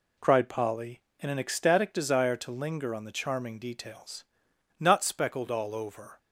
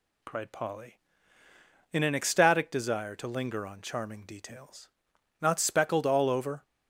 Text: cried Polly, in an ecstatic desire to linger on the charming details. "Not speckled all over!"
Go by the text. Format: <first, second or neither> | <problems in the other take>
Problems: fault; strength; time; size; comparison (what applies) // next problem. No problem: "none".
first | skips "the"; at 3.8 s